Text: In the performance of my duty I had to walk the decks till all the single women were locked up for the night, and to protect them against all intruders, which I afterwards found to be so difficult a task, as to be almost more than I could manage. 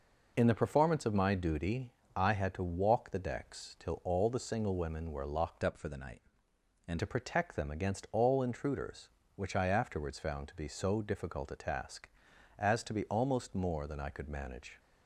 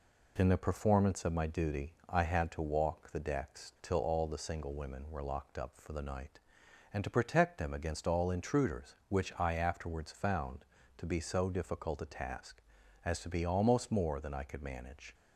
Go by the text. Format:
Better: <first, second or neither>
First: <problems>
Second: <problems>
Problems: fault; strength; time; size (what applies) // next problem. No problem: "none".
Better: second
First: pauses between "duty" and "I"; slight; at 1.9 s; 0.24 s long // changes voice from "up" to "and"; from 5.6 to 6.9 s; 1.3 s long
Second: pauses between "duty" and "I"; slight; at 1.9 s; 0.16 s long